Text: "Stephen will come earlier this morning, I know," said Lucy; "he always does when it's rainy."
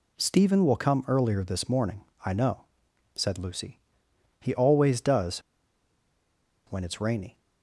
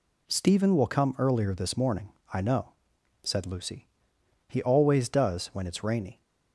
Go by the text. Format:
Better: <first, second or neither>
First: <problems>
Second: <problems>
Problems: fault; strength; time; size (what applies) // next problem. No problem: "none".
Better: second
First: pauses between "does" and "when"; strong; at 5.3 s; 1.2 s long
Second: none